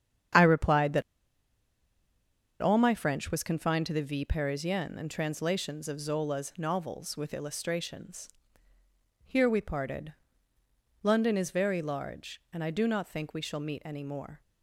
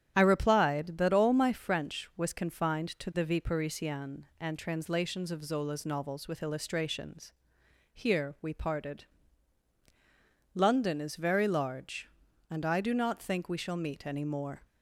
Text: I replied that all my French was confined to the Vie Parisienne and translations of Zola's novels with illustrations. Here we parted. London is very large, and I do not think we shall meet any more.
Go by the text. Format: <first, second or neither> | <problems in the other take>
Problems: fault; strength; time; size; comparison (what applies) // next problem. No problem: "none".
second | starts louder than the rest; strong; until 2.9 s; 8.5 dB; strong in the second // pauses between "that" and "all"; strong; at 1.0 s; 1.5 s long